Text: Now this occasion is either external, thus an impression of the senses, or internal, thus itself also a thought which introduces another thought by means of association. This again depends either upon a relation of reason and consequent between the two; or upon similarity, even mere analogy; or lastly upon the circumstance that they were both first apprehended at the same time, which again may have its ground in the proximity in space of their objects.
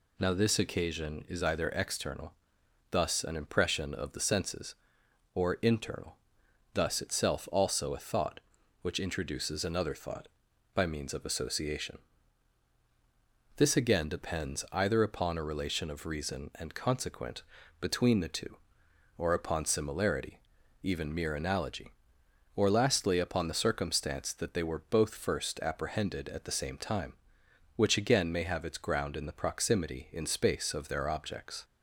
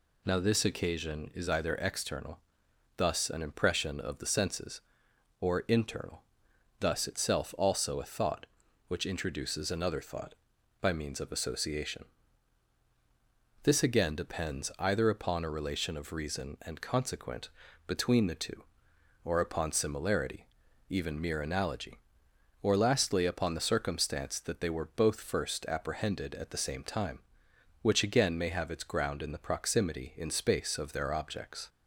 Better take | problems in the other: neither | pauses between "consequent" and "between"; the same in both

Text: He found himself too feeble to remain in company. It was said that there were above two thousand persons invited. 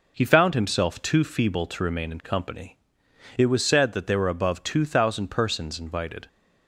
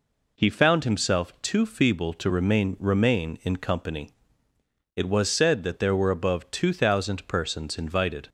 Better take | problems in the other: first | says "remain" twice; at 2.7 s

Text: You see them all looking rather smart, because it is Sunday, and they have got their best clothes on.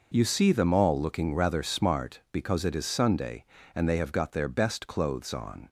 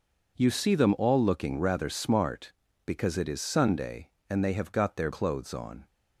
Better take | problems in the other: first | skips "best"; at 5.1 s

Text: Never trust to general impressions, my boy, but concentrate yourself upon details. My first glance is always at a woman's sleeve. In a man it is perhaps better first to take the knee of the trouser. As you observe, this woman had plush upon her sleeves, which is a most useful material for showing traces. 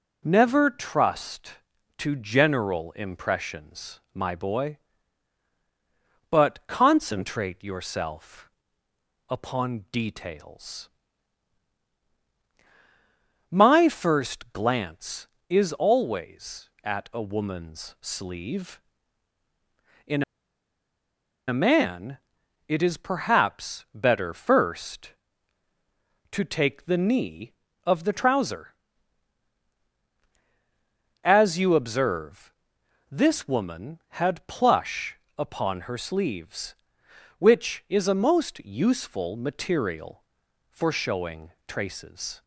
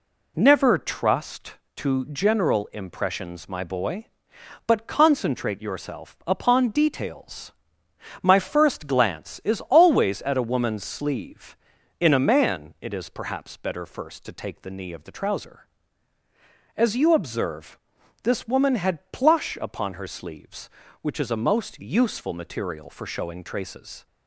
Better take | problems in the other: second | pauses between "yourself" and "upon"; noticeable; at 8.4 s; 0.80 s long // pauses between "In" and "a"; strong; at 20.2 s; 1.2 s long // pauses between "man" and "it"; noticeable; at 22.1 s; 0.48 s long // pauses between "plush" and "upon"; slight; at 35.1 s; 0.20 s long // pauses between "showing" and "traces"; slight; at 41.5 s; 0.16 s long

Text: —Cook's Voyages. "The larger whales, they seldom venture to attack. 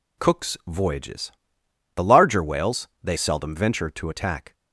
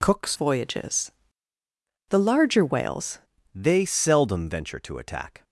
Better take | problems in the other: first | changes voice from "Voyages" to "whales"; from 0.3 to 3.1 s; 2.8 s long

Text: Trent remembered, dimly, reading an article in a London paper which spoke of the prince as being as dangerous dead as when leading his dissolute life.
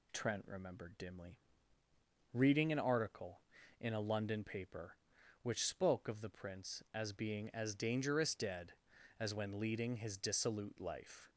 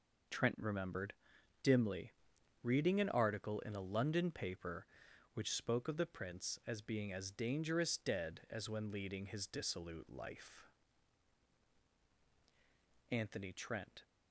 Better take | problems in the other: first | goes on to say "Anthony Trent"; noticeable; from 13.1 s on; 0.92 s long

